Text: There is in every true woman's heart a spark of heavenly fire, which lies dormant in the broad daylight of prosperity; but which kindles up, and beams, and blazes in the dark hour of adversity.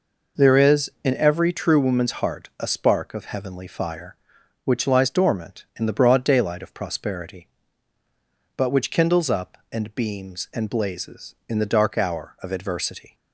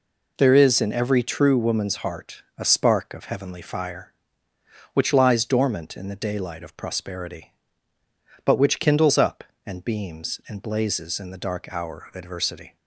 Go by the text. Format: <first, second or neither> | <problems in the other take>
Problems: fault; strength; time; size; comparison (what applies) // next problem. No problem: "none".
first | pauses between "heart" and "a"; slight; at 2.4 s; 0.16 s long // skips "broad"; at 6.2 s